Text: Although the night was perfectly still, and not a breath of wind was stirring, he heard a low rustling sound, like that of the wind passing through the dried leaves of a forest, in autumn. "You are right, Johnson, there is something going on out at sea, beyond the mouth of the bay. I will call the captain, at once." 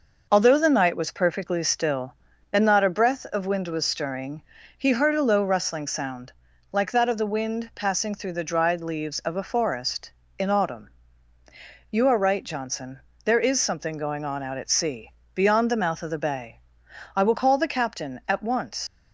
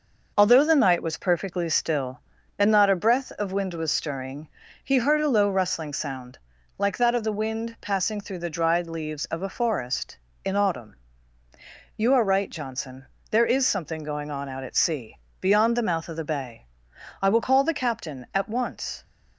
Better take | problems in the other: second | leaves "once" unfinished; at 18.8 s; 105 ms

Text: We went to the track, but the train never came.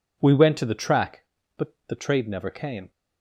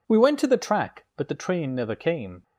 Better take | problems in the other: second | says "trade" for "train"; at 1.9 s

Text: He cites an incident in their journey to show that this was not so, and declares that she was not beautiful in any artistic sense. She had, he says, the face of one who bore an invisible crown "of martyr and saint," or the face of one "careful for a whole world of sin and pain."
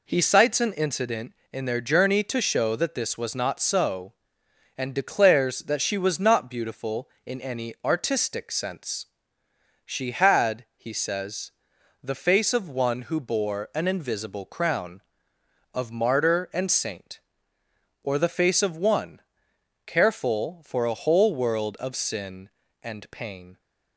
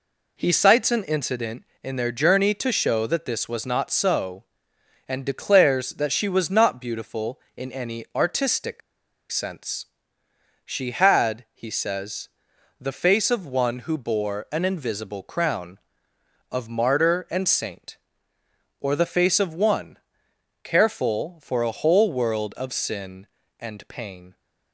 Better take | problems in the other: first | pauses between "artistic" and "sense"; noticeable; at 8.8 s; 0.52 s long // pauses between "one" and "careful"; noticeable; at 19.9 s; 0.64 s long; noticeable in the first

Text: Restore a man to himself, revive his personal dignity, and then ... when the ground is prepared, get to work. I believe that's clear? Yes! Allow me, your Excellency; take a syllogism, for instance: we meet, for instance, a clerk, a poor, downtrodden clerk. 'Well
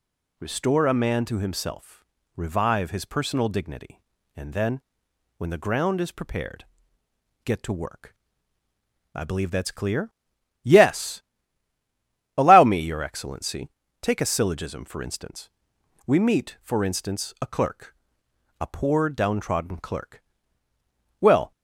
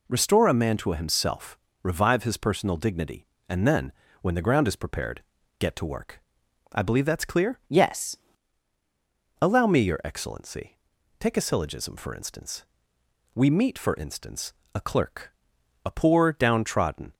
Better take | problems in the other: first | stops before "clerk Well"; at 17.1 s

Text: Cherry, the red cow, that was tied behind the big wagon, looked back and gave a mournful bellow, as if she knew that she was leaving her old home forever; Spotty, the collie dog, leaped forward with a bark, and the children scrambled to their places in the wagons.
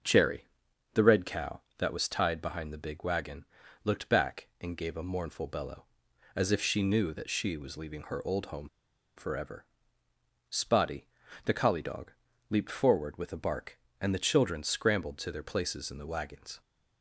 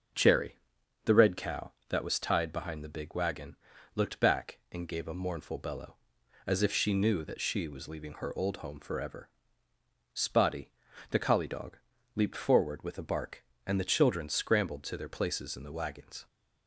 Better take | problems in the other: second | starts louder than the rest; until 1.5 s; 6.5 dB; also in the second // pauses between "home" and "forever"; noticeable; at 8.6 s; 0.47 s long

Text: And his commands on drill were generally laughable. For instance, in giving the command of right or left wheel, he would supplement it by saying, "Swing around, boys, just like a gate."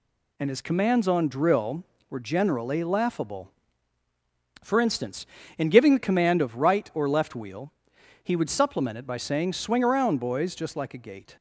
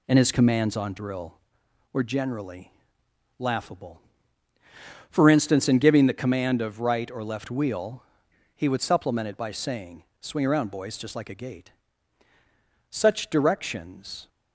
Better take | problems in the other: first | pauses between "generally" and "laughable"; noticeable; at 2.7 s; 0.66 s long // goes on to say "Such directions"; from 12.9 s on; 1.3 s long

